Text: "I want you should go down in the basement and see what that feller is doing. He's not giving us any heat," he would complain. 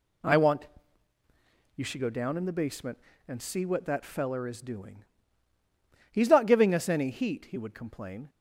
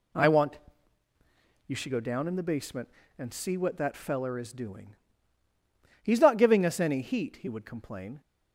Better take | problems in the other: neither | pauses between "want" and "you"; the same in both

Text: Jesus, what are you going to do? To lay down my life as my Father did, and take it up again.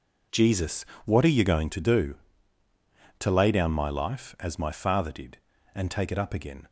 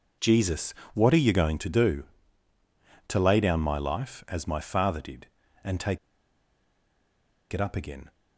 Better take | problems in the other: first | pauses between "take" and "it"; strong; at 5.9 s; 1.5 s long

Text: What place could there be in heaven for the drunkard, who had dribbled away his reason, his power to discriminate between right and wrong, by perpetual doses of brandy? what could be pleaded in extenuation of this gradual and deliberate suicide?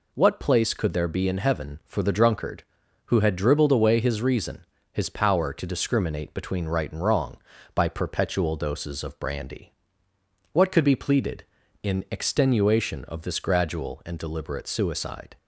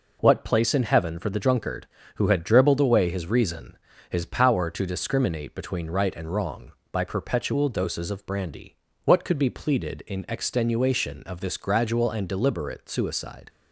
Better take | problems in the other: first | skips "could there be"; at 0.7 s

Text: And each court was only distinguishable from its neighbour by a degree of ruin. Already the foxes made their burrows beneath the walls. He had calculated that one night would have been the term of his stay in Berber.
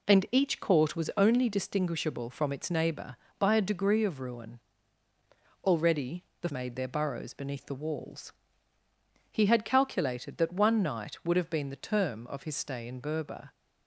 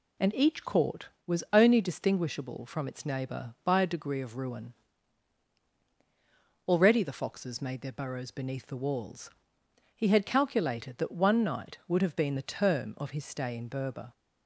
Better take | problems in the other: second | pauses between "Already" and "the"; slight; at 6.2 s; 0.18 s long // skips "foxes"; at 6.5 s

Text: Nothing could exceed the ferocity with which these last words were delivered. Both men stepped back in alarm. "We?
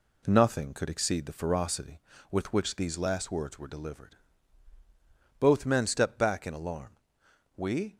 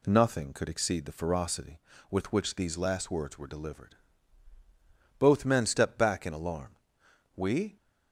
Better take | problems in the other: second | gets quieter; noticeable; throughout; 4 dB

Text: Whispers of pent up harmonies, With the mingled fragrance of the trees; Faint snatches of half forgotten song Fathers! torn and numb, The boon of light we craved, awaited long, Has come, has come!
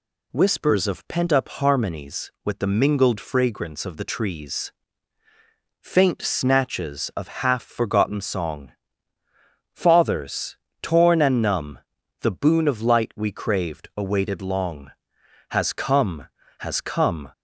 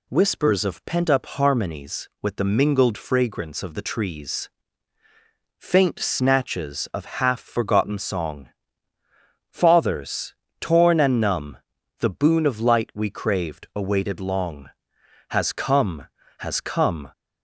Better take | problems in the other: neither | pauses between "song" and "Fathers"; the same in both

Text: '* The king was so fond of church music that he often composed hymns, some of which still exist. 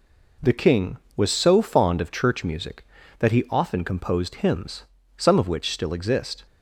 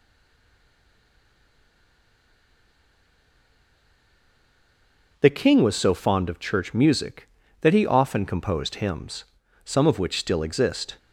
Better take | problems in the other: first | stays silent before the first word; strong; until 5.1 s; 5.1 s long

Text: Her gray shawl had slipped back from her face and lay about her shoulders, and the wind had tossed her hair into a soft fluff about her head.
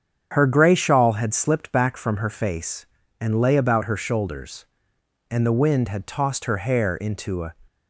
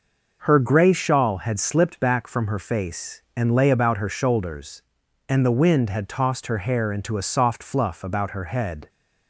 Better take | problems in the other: second | starts louder than the rest; strong; until 1.3 s; 7.5 dB // stops before "soft fluff about her head"; at 7.6 s

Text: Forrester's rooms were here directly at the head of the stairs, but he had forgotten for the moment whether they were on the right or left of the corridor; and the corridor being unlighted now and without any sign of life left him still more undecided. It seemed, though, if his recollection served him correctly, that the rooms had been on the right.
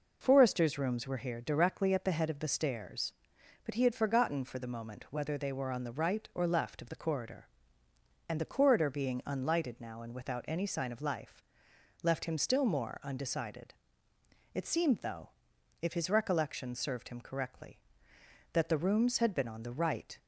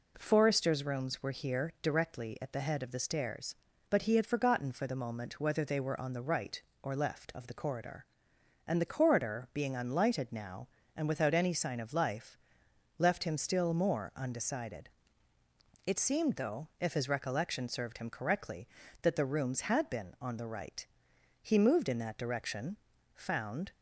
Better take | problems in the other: first | pauses between "life" and "left"; noticeable; at 12.3 s; 0.60 s long; noticeable in the first // goes on to say "He moved in that direction found"; strong; from 21.4 s on; 2.3 s long

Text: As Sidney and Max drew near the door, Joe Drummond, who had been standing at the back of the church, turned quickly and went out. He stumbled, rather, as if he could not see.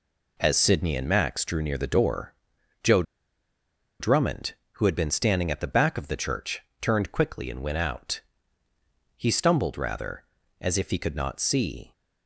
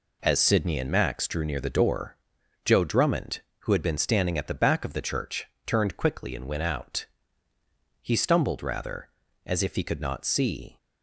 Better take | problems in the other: second | pauses between "Joe" and "Drummond"; noticeable; at 3.0 s; 0.96 s long

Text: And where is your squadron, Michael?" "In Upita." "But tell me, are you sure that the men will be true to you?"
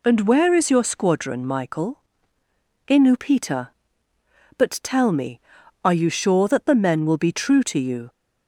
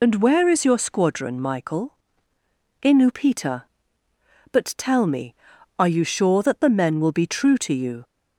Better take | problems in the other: first | loses the start of "And"; at 0.0 s; 35 ms

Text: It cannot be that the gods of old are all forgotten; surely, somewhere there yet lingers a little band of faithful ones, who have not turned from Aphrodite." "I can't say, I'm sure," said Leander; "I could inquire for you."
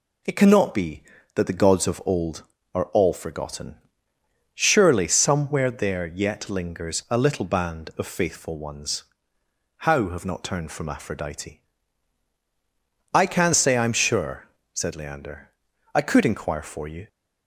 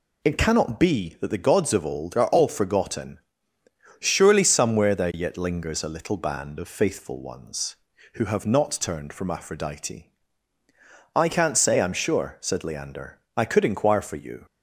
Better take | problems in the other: second | says "how" for "who"; at 9.7 s

